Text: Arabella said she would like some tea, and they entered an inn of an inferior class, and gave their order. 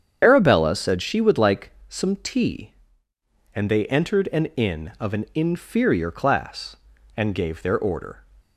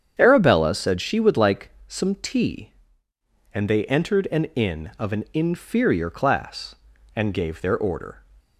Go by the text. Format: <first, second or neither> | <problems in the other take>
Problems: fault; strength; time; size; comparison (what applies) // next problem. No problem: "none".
second | loses the start of "Arabella"; at 0.2 s; 25 ms // starts louder than the rest; strong; until 1.2 s; 8 dB; strong in the second // pauses between "like" and "some"; slight; at 1.6 s; 0.18 s long; slight in the second